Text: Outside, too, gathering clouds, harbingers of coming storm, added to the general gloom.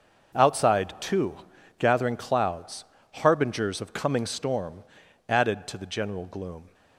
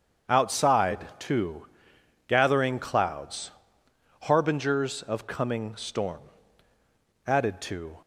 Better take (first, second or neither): first